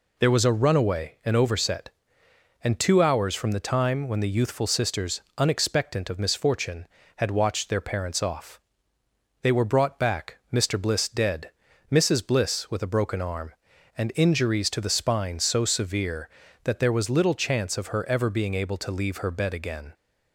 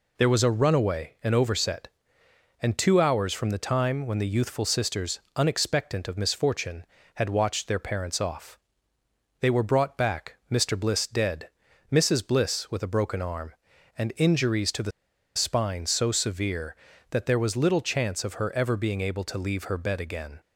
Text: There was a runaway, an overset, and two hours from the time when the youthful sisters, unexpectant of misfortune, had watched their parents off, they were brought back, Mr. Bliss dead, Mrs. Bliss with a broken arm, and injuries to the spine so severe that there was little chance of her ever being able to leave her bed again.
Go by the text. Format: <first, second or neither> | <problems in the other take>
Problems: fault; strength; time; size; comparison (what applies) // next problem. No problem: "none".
first | pauses between "the" and "spine"; at 14.9 s; 0.45 s long